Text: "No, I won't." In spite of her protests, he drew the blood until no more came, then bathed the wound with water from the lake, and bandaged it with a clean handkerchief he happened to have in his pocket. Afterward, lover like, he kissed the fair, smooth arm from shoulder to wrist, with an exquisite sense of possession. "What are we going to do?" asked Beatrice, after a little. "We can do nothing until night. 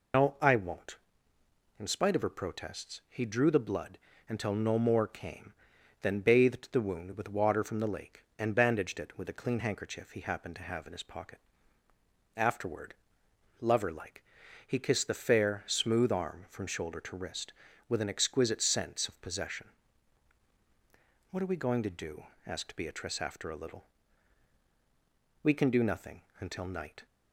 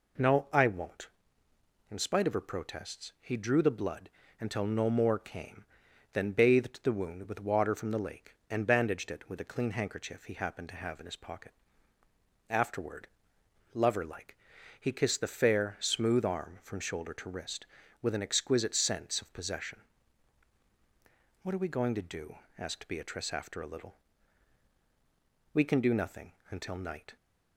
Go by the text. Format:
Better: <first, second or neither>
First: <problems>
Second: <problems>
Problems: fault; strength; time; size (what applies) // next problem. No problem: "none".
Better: second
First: loses the start of "No"; at 0.1 s; 105 ms // pauses between "blood" and "until"; slight; at 3.9 s; 0.32 s long // pauses between "nothing" and "until"; slight; at 26.2 s; 0.18 s long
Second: pauses between "blood" and "until"; slight; at 4.0 s; 0.32 s long // pauses between "nothing" and "until"; slight; at 26.3 s; 0.18 s long